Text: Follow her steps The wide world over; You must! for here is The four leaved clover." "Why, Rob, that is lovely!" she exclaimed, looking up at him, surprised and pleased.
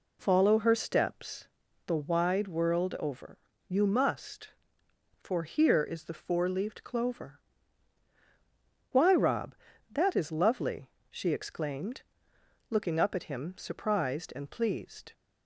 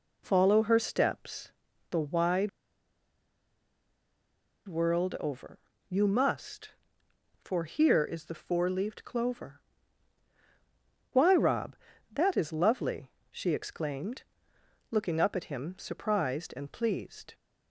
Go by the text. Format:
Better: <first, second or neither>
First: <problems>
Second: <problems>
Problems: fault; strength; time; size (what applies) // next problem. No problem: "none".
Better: first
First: pauses between "steps" and "The"; at 1.4 s; 0.38 s long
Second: pauses between "steps" and "The"; at 1.5 s; 0.38 s long // pauses between "wide" and "world"; strong; at 2.4 s; 2.1 s long